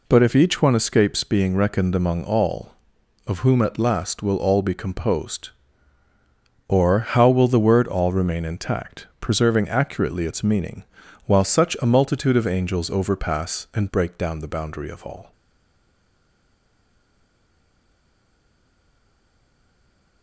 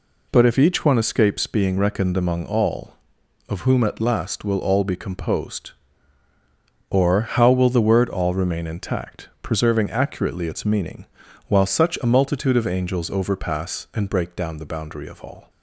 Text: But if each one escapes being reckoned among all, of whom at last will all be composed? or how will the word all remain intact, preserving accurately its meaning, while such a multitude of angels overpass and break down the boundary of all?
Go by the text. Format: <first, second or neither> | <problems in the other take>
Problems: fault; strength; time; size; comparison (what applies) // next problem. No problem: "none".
second | stays silent after the last word; strong; from 15.3 s on; 4.9 s long